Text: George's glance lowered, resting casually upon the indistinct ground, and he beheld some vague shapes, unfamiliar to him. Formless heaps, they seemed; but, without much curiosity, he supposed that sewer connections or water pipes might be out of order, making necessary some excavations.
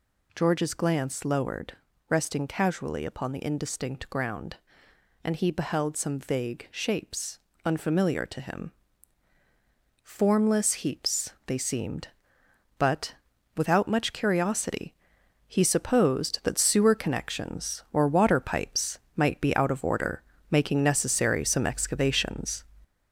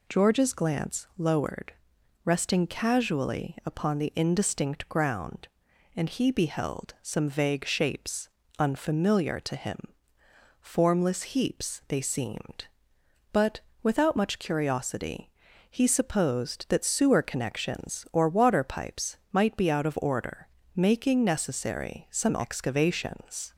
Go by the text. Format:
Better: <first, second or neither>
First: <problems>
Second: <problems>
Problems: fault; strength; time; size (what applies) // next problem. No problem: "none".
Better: second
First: gets louder; noticeable; throughout; 4.5 dB // pauses between "pipes" and "might"; slight; at 18.9 s; 0.18 s long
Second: pauses between "pipes" and "might"; slight; at 19.1 s; 0.16 s long